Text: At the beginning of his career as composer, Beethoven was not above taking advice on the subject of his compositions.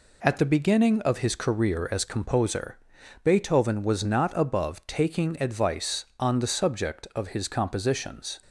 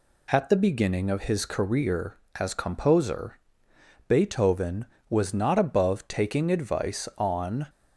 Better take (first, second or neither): first